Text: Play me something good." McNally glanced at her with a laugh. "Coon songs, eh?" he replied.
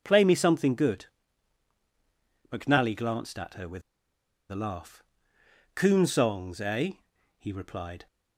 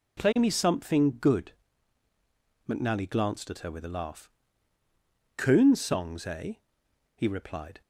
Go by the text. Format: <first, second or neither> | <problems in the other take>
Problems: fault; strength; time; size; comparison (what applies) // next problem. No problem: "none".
second | pauses between "with" and "a"; noticeable; at 3.8 s; 0.68 s long